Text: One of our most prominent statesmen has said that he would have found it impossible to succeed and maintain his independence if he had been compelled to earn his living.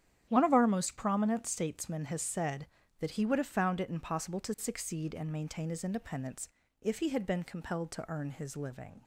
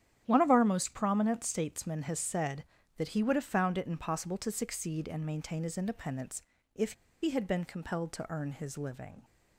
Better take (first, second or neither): first